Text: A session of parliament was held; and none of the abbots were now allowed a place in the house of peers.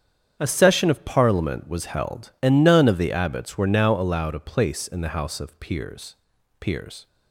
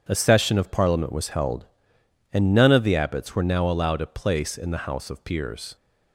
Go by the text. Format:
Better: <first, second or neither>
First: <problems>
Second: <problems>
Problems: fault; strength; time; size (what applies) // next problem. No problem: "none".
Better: second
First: starts louder than the rest; strong; until 1.4 s; 8 dB // says "peers" twice; at 6.5 s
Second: none